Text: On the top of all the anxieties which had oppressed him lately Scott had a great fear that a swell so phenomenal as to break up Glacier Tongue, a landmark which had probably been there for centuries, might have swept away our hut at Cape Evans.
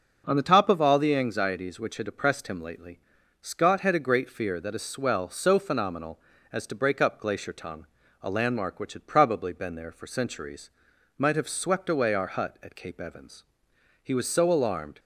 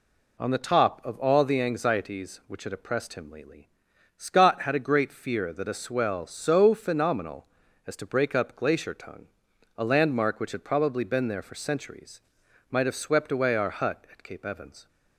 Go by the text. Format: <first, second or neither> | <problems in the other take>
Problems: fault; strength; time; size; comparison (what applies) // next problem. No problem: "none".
second | pauses between "lately" and "Scott"; at 2.9 s; 0.42 s long; noticeable in the second // goes on to say "He was so alarmed"; noticeable; from 14.0 s on; 0.96 s long